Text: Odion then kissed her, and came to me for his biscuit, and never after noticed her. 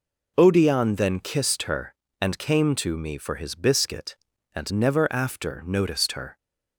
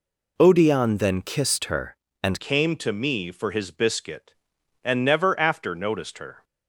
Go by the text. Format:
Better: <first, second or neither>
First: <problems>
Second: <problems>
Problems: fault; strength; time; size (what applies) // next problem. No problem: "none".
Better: first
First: none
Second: changes voice at "came"; from 2.3 s on; 4.1 s long